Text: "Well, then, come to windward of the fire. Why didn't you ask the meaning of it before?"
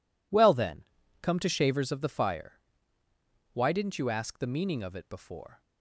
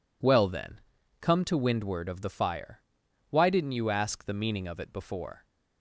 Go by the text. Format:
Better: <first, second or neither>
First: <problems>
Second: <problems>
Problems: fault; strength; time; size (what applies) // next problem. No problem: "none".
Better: second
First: says "shavers" for "windward"; at 1.4 s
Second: none